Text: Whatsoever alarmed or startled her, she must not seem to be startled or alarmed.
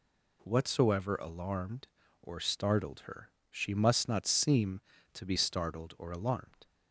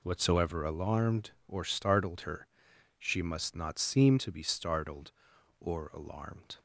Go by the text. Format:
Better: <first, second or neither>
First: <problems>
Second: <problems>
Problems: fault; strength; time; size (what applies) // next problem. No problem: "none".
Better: neither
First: none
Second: none